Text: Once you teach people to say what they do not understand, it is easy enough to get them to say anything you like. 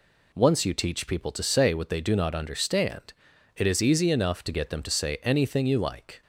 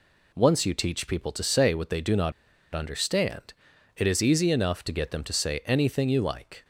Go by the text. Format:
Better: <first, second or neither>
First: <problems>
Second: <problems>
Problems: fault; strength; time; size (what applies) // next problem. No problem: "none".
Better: first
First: none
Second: pauses between "not" and "understand"; at 2.3 s; 0.42 s long